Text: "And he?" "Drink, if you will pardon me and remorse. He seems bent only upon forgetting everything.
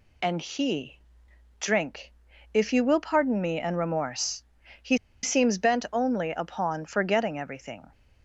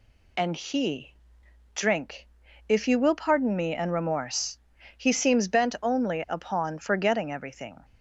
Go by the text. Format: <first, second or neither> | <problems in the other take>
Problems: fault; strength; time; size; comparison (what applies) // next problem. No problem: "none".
second | pauses between "He" and "seems"; slight; at 4.9 s; 0.26 s long